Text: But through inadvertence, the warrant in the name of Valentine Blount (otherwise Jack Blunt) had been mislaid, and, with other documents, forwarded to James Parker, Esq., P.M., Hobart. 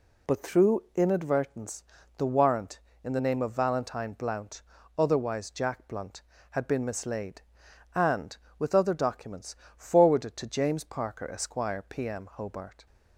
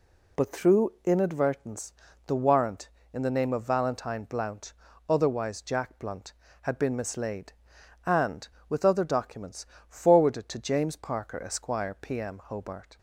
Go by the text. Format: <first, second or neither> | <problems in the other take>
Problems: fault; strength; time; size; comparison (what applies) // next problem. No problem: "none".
neither | none